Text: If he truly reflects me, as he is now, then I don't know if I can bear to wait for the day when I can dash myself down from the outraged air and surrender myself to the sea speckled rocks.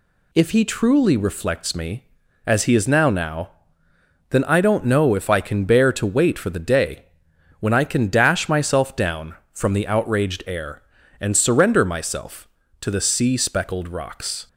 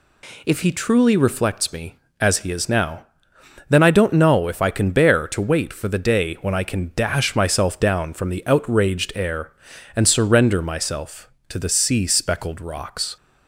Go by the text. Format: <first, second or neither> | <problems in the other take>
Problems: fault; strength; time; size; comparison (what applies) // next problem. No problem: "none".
second | says "now" twice; at 3.0 s // pauses between "day" and "when"; noticeable; at 7.0 s; 0.56 s long